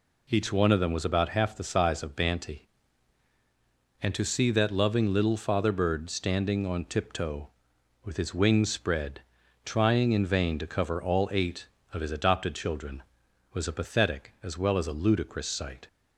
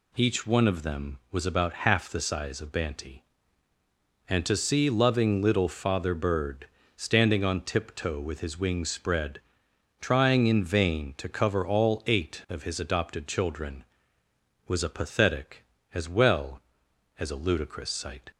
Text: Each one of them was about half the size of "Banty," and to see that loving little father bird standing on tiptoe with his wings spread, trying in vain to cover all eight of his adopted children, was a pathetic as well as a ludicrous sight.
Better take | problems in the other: first | skips "that"; at 4.9 s // pauses between "bird" and "standing"; slight; at 6.6 s; 0.28 s long

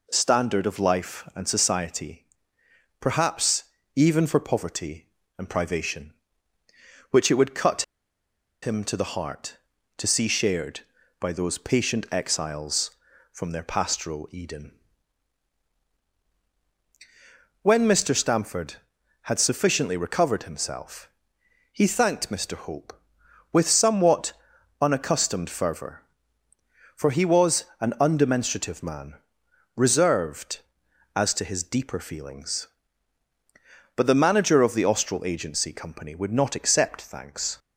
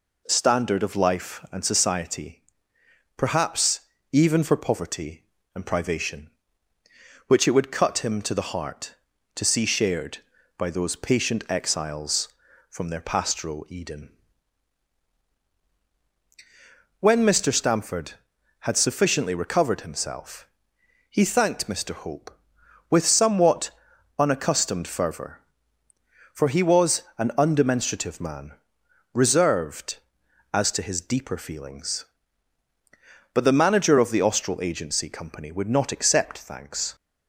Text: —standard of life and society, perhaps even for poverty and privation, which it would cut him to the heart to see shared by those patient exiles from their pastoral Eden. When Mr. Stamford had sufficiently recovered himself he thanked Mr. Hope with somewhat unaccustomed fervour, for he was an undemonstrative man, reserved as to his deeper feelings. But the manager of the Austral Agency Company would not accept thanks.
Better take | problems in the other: second | pauses between "perhaps" and "even"; slight; at 3.6 s; 0.30 s long; slight in the second // pauses between "cut" and "him"; noticeable; at 7.8 s; 0.79 s long // pauses between "himself" and "he"; noticeable; at 21.0 s; 0.64 s long; noticeable in the second // pauses between "somewhat" and "unaccustomed"; noticeable; at 24.3 s; 0.48 s long; noticeable in the second // pauses between "was" and "an"; slight; at 27.6 s; 0.16 s long; slight in the second

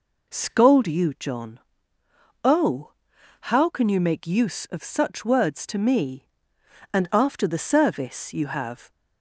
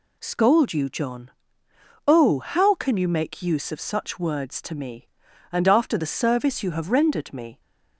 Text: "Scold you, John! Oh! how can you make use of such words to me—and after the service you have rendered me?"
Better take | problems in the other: second | stops before "rendered me"; at 8.8 s

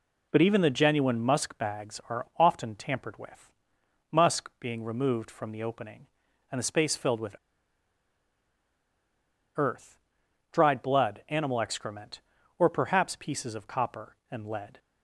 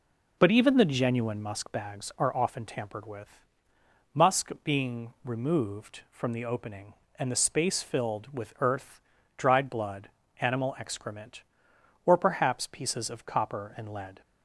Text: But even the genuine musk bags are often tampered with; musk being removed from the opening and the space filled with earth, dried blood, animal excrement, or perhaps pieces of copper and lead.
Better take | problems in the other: second | pauses between "with" and "earth"; strong; at 7.3 s; 2.2 s long

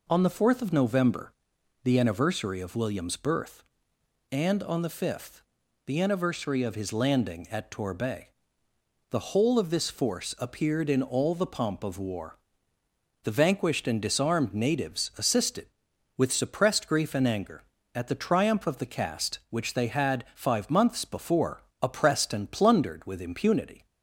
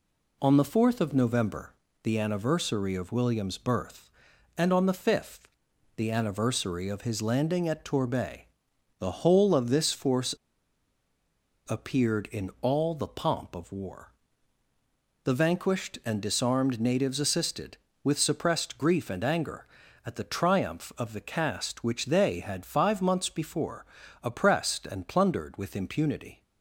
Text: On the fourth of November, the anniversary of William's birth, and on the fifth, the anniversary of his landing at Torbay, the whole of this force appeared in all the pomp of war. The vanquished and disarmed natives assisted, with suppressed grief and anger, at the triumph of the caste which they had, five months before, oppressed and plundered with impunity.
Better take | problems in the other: first | pauses between "force" and "appeared"; strong; at 10.3 s; 1.3 s long

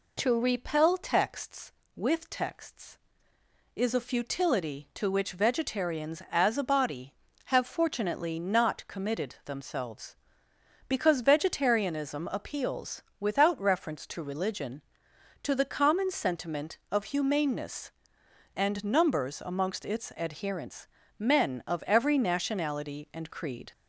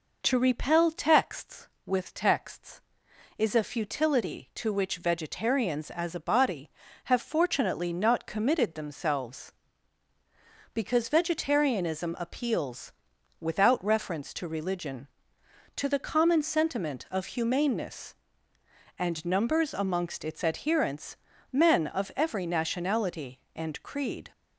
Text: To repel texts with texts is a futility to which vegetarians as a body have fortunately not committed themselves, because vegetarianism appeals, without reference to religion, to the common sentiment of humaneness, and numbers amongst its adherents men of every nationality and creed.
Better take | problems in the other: neither | pauses between "adherents" and "men"; slight; the same in both

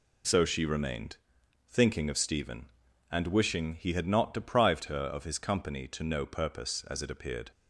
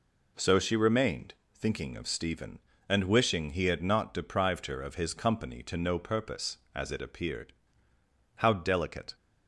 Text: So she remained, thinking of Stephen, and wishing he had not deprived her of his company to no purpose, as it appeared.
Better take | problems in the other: first | goes on to say "How delicate"; noticeable; from 8.3 s on; 0.78 s long

